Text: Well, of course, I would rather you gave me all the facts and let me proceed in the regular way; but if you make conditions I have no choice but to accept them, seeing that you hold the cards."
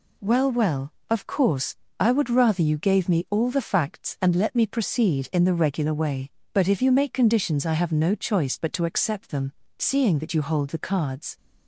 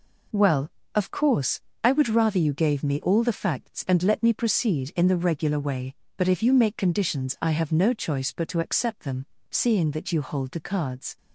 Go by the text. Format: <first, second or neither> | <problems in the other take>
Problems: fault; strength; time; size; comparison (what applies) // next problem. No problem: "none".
second | says "Well" twice; at 0.5 s